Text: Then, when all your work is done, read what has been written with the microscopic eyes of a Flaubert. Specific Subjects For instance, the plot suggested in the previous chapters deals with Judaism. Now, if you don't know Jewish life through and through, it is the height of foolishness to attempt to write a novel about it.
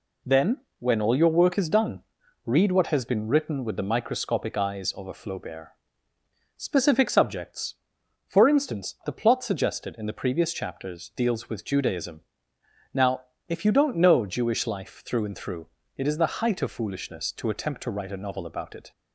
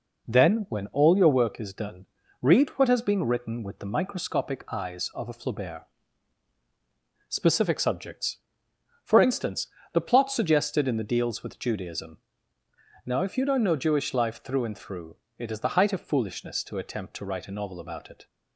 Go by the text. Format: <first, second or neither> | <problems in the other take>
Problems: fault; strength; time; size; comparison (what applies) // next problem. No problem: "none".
first | skips "previous chapters"; at 11.0 s